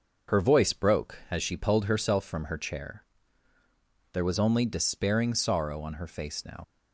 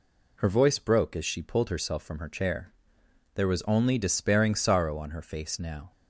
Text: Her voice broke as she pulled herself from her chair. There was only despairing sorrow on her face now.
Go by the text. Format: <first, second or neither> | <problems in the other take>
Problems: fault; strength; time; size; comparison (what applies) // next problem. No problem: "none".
second | starts louder than the rest; until 1.4 s; 6 dB // leaves "now" unfinished; at 6.6 s; 50 ms